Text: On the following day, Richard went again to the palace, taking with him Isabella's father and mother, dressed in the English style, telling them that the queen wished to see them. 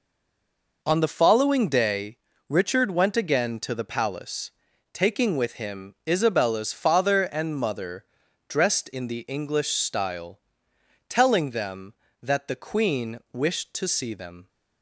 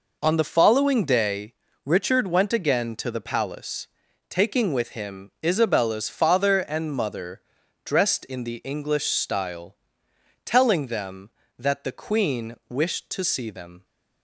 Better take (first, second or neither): second